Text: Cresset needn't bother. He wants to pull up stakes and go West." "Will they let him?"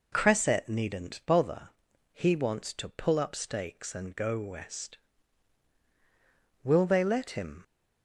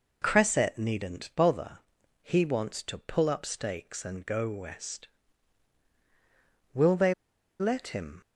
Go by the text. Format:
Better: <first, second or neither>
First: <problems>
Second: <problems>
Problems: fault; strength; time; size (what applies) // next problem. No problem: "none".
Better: first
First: none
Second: pauses between "they" and "let"; noticeable; at 7.1 s; 0.47 s long